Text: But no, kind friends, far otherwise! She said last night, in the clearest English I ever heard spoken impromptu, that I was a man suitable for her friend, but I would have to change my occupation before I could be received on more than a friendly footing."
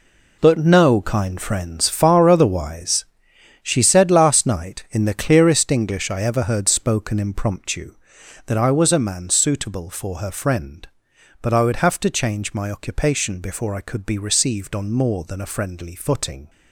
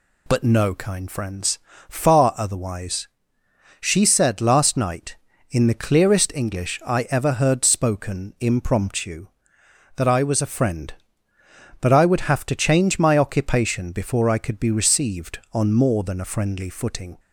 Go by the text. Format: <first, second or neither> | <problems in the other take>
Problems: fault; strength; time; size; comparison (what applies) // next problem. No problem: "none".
first | skips "man suitable for her"; at 10.5 s